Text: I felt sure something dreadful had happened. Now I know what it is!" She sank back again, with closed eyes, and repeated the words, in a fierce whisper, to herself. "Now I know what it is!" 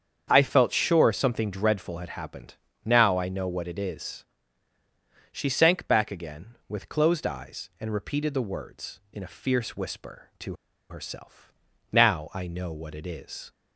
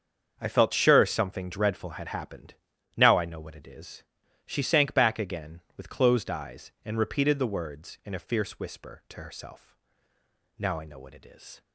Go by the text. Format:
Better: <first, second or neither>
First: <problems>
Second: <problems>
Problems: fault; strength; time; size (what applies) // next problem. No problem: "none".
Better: second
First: starts louder than the rest; strong; until 1.3 s; 7.5 dB // pauses between "to" and "herself"; at 10.5 s; 0.37 s long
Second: starts louder than the rest; until 1.4 s; 7 dB